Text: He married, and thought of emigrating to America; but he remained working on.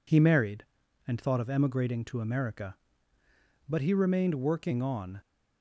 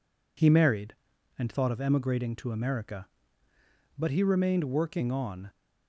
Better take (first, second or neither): neither